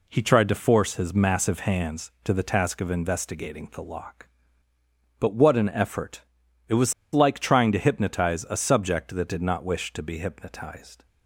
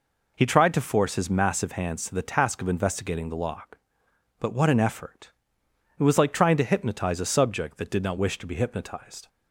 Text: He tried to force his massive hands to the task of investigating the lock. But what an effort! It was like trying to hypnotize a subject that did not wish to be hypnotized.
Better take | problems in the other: second | pauses between "was" and "like"; slight; at 6.9 s; 0.20 s long

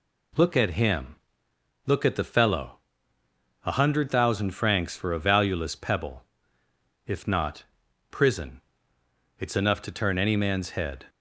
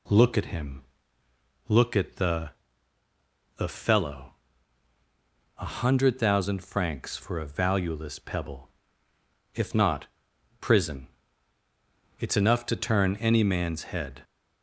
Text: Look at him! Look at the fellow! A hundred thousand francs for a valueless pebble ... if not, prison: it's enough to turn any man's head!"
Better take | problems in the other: first | says "the" twice; at 3.5 s

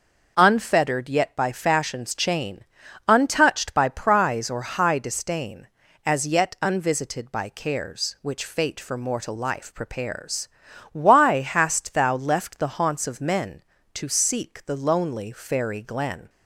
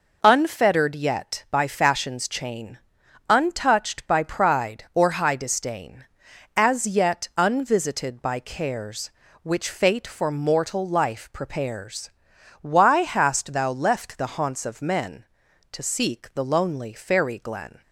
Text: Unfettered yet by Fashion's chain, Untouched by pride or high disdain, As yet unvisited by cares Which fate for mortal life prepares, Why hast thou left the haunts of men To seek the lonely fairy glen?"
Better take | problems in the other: second | says "prize" for "pride"; at 3.8 s

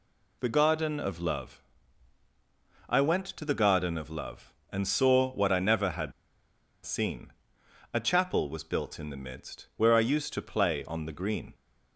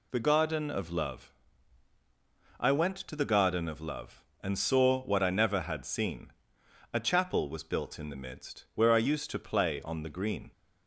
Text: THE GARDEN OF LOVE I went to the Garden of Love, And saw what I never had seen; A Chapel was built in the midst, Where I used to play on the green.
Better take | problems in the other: second | pauses between "LOVE" and "I"; strong; at 1.6 s; 1.2 s long; strong in the second // pauses between "had" and "seen"; noticeable; at 6.1 s; 0.74 s long

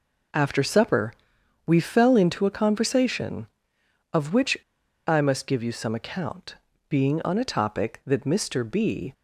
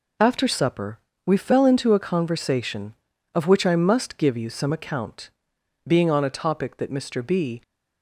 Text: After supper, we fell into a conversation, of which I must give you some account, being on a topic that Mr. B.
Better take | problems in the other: second | pauses between "which" and "I"; noticeable; at 4.5 s; 0.51 s long

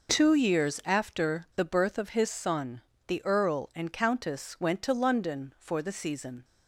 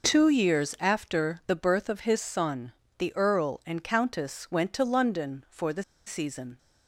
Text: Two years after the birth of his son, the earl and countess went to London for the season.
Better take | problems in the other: first | pauses between "the" and "season"; slight; at 5.8 s; 0.25 s long

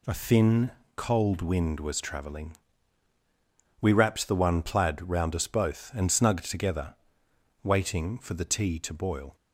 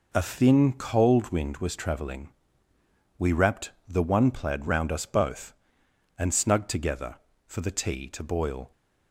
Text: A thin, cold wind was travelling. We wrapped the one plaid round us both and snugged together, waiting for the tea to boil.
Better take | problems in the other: first | pauses between "wrapped" and "the"; slight; at 3.7 s; 0.16 s long // skips "waiting"; at 7.3 s

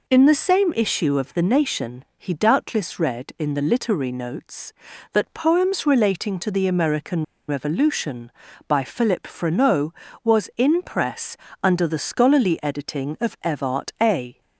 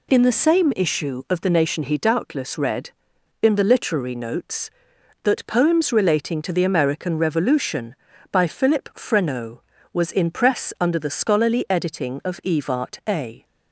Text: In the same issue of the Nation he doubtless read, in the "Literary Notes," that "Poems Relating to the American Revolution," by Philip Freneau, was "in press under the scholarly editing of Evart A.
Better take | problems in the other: second | pauses between "American" and "Revolution"; slight; at 7.2 s; 0.23 s long // pauses between "press" and "under"; slight; at 11.3 s; 0.28 s long

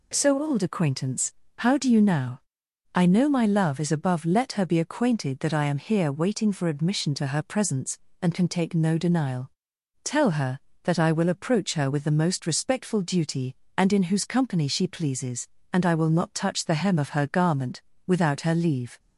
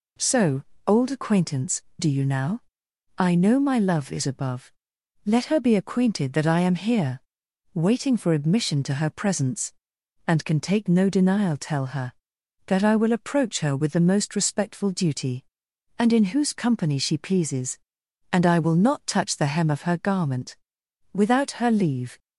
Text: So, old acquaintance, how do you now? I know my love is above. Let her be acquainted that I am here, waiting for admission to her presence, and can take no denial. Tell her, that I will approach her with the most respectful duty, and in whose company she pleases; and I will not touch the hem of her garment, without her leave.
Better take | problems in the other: first | skips "how"; at 1.9 s

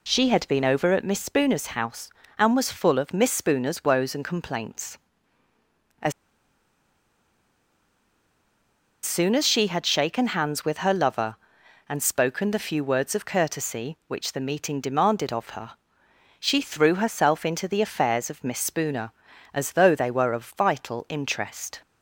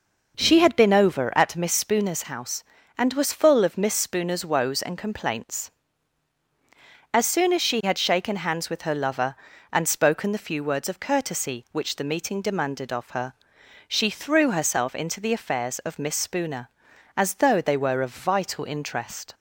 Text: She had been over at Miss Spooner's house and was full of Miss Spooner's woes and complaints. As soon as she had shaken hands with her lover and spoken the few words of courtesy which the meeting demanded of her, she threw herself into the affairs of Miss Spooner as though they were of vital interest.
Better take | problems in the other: second | pauses between "As" and "soon"; strong; at 6.1 s; 2.9 s long

